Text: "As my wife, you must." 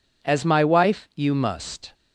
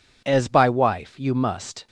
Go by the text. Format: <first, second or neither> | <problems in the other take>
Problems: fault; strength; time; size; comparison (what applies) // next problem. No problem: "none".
first | says "by" for "my"; at 0.4 s